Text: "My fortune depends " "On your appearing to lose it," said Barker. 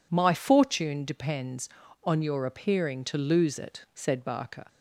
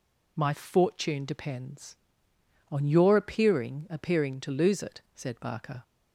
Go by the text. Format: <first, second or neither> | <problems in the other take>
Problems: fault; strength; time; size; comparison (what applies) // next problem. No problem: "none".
first | says "appearing" twice; at 3.8 s